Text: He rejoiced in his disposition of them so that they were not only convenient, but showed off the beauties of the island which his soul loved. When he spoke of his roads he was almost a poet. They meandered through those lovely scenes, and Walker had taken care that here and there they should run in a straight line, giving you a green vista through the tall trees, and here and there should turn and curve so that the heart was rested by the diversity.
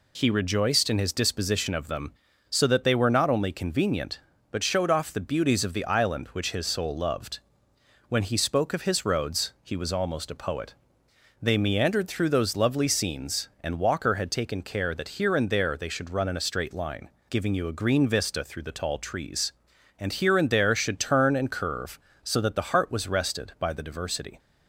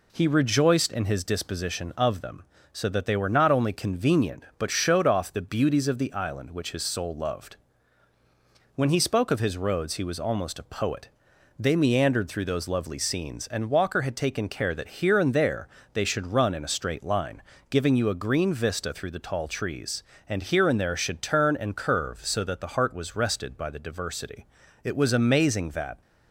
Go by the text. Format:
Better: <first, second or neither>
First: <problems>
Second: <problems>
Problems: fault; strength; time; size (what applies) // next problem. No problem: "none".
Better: first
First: none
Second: pauses between "there" and "they"; slight; at 15.6 s; 0.26 s long // goes on to say "It was amazing that"; noticeable; from 24.8 s on; 1.1 s long